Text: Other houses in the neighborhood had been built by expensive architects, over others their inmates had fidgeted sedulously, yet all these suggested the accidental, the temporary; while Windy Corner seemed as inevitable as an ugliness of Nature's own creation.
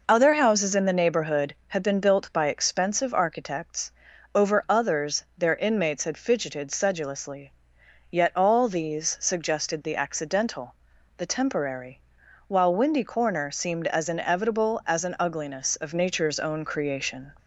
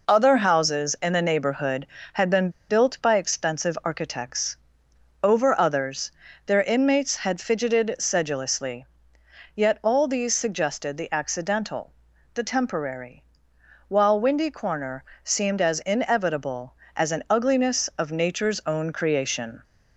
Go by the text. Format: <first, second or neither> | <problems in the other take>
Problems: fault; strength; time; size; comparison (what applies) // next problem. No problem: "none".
first | pauses between "been" and "built"; slight; at 2.4 s; 0.20 s long // pauses between "others" and "their"; slight; at 6.1 s; 0.36 s long // pauses between "Corner" and "seemed"; slight; at 15.0 s; 0.18 s long